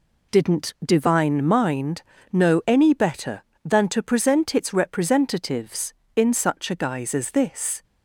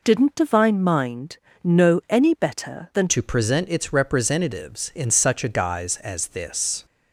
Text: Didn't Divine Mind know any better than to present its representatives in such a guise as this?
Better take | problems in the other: first | pauses between "Mind" and "know"; slight; at 1.3 s; 0.26 s long; slight in the first // changes voice at "to"; from 3.0 s on; 3.8 s long

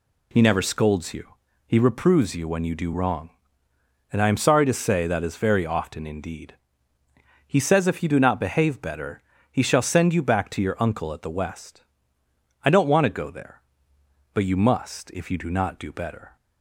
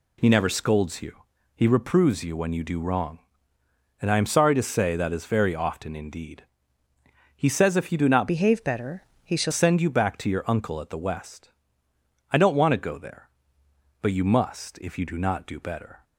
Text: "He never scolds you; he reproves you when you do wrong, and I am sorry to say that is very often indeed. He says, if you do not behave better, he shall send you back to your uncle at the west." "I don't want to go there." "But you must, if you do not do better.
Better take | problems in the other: first | changes voice from "behave" to "shall"; from 8.2 to 9.5 s; 1.3 s long

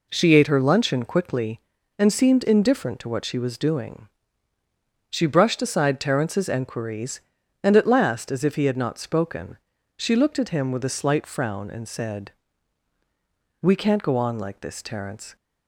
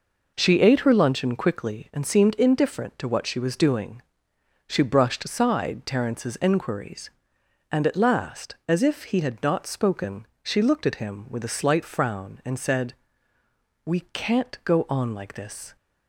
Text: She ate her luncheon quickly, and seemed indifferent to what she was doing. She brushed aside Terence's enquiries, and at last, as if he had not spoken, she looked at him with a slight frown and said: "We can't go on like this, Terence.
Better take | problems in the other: first | stops before "Terence"; at 15.7 s

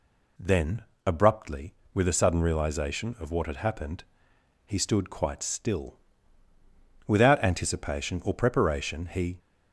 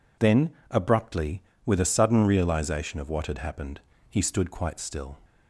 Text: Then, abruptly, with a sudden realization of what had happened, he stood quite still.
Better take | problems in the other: second | goes on to say "Without anticipation or preparation he"; strong; from 7.0 s on; 2.3 s long

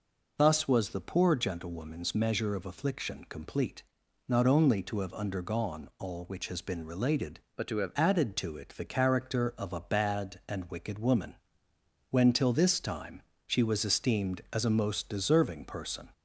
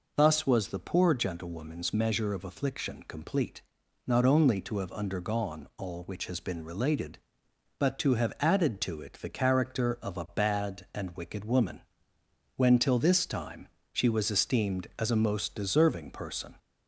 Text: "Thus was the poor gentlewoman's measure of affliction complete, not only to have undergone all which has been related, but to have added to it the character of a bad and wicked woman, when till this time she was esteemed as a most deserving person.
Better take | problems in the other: second | changes voice from "but" to "have"; from 7.5 to 7.9 s; 0.4 s long // pauses between "time" and "she"; slight; at 13.2 s; 0.24 s long; slight in the second

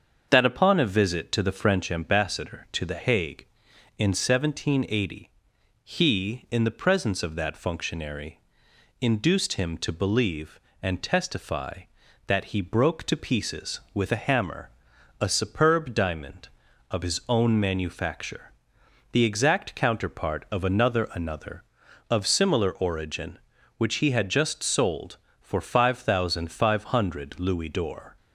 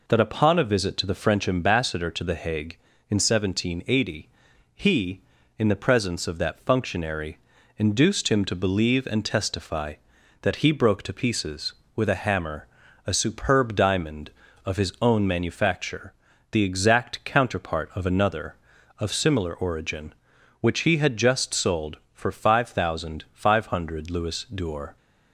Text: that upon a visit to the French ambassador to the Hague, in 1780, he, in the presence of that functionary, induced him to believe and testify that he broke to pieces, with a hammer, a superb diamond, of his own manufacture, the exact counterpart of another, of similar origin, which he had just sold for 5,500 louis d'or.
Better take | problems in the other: second | starts louder than the rest; until 1.3 s; 7 dB // says "another" twice; at 21.1 s

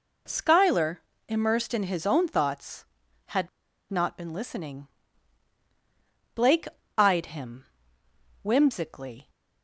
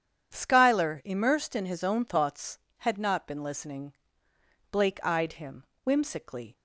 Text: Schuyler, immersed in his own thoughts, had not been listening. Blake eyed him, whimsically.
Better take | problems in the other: second | pauses between "had" and "not"; at 3.4 s; 0.41 s long // pauses between "Blake" and "eyed"; slight; at 6.6 s; 0.30 s long

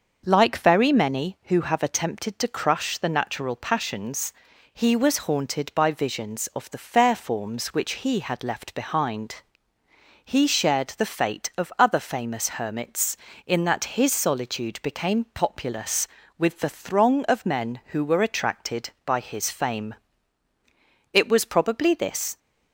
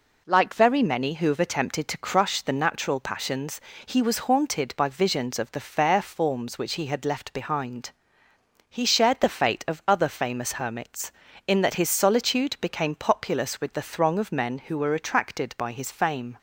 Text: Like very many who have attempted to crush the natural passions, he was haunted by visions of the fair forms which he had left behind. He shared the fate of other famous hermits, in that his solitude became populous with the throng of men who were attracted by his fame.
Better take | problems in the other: second | starts louder than the rest; until 1.2 s; 6.5 dB // goes on to say "It was probably this"; noticeable; from 21.1 s on; 1.2 s long

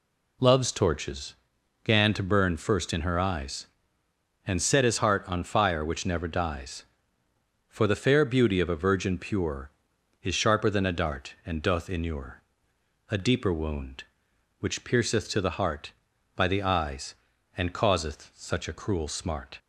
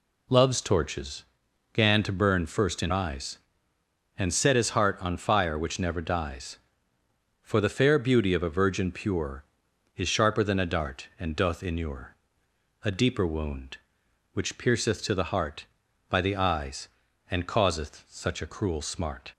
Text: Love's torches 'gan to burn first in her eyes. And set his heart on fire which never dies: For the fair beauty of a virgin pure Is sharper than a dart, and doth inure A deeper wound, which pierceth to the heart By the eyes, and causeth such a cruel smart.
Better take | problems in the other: first | pauses between "torches" and "gan"; noticeable; at 1.2 s; 0.50 s long; noticeable in the first // skips "her"; at 2.9 s // pauses between "inure" and "A"; noticeable; at 12.1 s; 0.66 s long; noticeable in the first

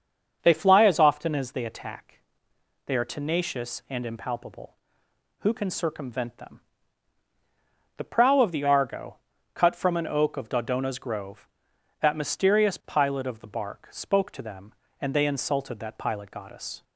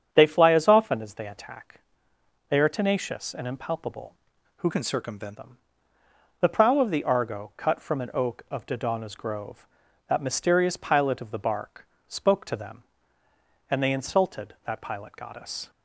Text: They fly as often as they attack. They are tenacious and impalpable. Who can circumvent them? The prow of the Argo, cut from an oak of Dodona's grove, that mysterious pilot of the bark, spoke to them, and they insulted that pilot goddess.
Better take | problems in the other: first | starts louder than the rest; strong; until 1.1 s; 8 dB; also in the first // changes voice from "can" to "circumvent"; from 4.7 to 5.3 s; 0.6 s long

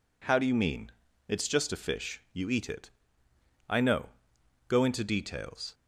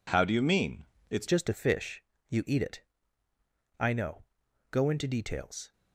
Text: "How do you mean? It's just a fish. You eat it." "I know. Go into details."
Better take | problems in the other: first | changes voice at "just"; from 1.2 s on; 4.5 s long

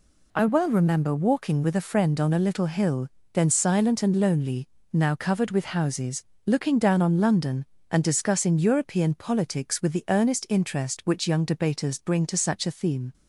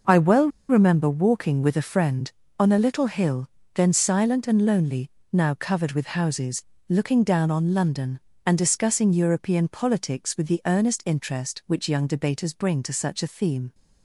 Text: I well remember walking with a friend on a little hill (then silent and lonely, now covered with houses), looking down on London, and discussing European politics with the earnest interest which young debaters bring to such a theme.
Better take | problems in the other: first | pauses between "well" and "remember"; slight; at 0.4 s; 0.21 s long

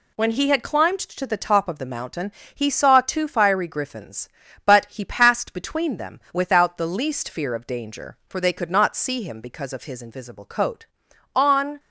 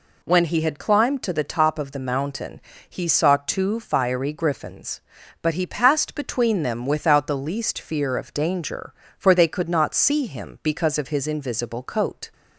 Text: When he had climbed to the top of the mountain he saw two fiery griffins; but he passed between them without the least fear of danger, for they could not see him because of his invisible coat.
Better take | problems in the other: second | pauses between "mountain" and "he"; slight; at 2.3 s; 0.22 s long; slight in the second // goes on to say "On"; slight; from 11.3 s on; 0.44 s long

